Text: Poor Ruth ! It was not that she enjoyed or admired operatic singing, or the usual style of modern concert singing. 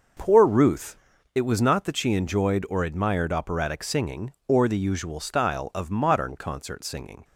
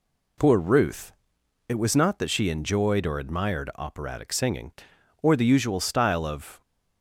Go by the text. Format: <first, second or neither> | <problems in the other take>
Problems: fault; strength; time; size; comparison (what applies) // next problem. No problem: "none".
first | stops before "modern concert singing"; at 6.6 s